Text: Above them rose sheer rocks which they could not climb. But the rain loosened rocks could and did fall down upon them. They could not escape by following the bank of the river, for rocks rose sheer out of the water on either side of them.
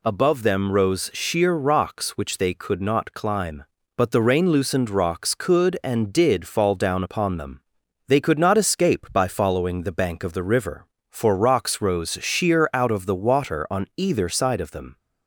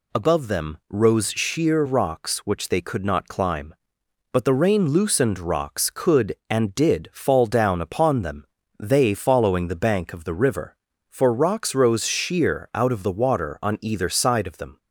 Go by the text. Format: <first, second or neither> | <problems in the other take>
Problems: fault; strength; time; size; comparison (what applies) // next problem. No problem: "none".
first | skips "could not escape by"; at 9.1 s